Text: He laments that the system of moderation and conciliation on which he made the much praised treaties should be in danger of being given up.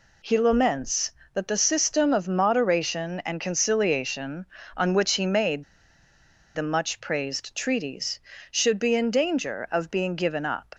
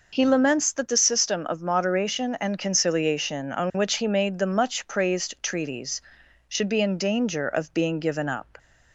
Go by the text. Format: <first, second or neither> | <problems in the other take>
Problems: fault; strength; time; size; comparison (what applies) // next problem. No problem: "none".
second | pauses between "made" and "the"; noticeable; at 5.6 s; 0.90 s long